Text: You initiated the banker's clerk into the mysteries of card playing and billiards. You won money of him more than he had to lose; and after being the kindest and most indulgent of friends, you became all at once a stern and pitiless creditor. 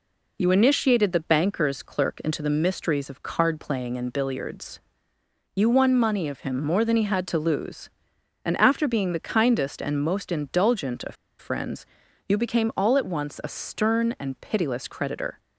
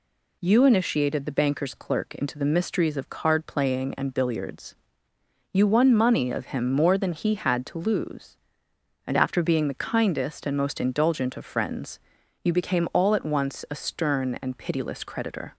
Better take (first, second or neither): second